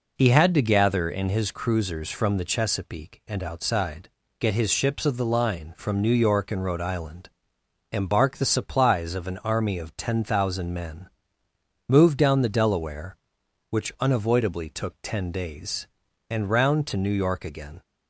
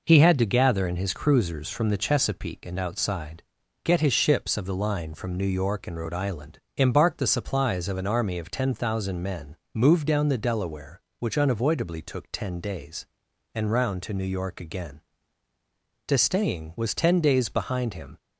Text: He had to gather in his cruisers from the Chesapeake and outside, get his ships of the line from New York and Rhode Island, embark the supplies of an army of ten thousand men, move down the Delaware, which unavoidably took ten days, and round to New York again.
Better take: first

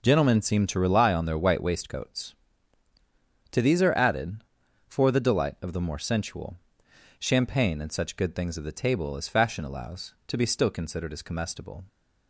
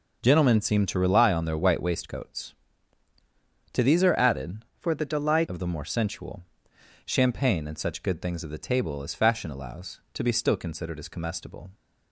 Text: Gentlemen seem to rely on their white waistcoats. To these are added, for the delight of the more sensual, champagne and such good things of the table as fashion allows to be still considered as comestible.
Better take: first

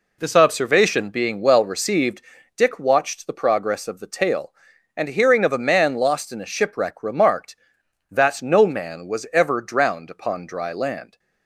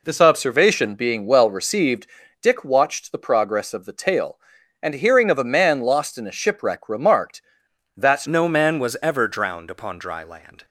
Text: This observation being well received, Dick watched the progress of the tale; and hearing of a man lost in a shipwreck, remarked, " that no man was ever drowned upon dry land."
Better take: first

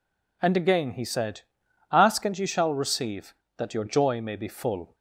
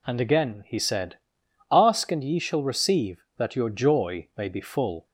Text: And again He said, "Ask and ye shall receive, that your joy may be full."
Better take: neither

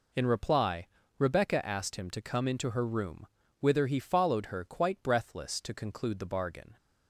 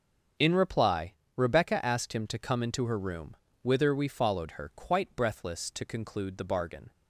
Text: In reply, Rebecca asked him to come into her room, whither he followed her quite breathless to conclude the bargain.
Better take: first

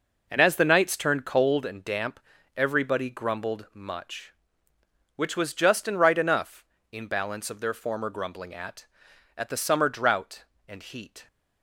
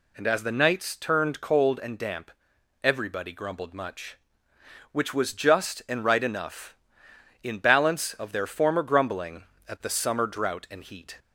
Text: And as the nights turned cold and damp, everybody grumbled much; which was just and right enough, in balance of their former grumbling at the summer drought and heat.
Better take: second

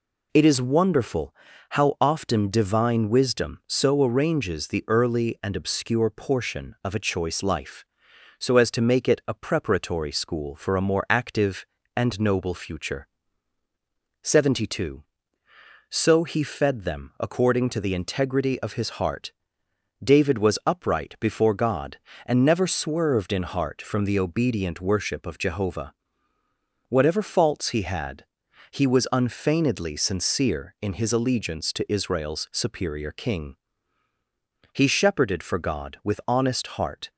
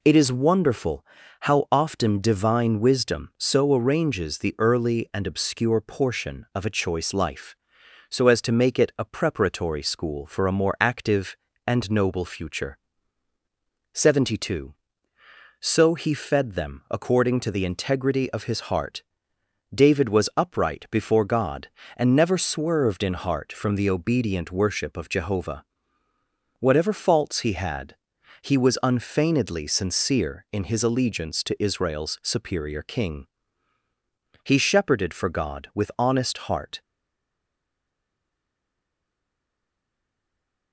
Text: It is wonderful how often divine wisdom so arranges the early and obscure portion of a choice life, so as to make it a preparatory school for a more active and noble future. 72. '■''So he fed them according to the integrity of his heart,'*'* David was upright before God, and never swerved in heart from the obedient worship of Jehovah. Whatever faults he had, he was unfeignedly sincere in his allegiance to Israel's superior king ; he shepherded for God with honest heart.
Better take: first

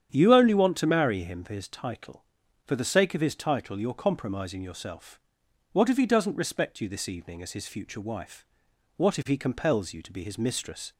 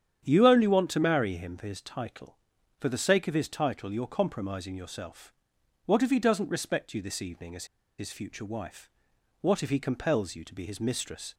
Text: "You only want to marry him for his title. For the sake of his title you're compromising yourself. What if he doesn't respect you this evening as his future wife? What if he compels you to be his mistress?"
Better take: first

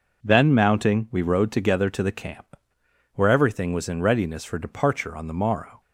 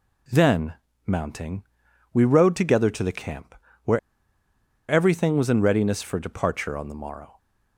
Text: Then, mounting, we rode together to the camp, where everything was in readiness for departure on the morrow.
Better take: first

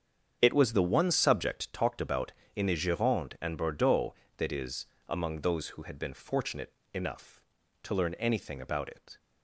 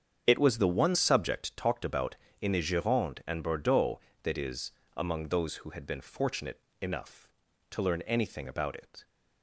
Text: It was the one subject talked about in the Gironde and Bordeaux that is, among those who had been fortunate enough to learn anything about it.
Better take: neither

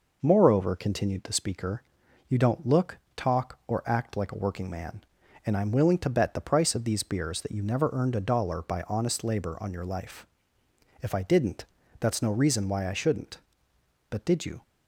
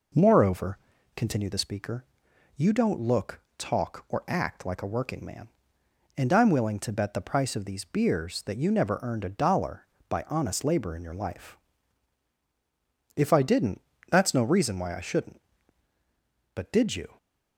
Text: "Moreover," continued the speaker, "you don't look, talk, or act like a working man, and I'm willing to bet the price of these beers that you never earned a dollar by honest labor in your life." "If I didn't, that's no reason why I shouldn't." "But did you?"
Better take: second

